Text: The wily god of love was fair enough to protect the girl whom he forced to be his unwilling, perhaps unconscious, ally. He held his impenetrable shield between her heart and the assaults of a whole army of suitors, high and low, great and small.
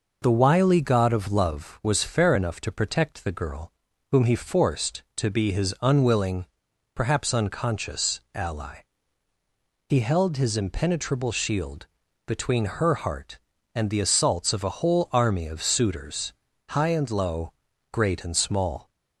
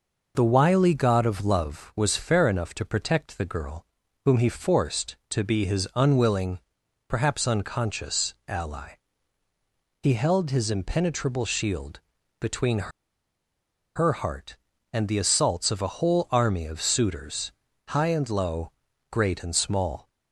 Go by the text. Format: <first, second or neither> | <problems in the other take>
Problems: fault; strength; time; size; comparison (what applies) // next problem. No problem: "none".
first | pauses between "girl" and "whom"; at 3.8 s; 0.40 s long; also in the first // pauses between "shield" and "between"; at 11.9 s; 0.38 s long; also in the first // pauses between "between" and "her"; at 12.8 s; 1.0 s long